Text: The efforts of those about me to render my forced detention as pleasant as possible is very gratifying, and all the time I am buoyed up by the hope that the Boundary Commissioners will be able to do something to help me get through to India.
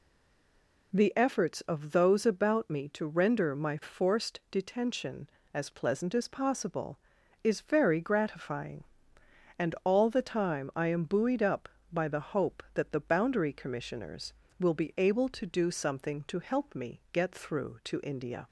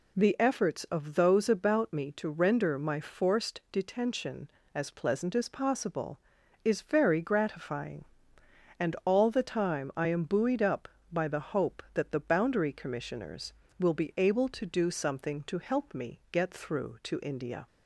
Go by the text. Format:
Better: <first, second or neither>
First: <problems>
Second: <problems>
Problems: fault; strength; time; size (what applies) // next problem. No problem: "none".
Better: second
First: stays silent before the first word; slight; until 0.9 s; 0.9 s long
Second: none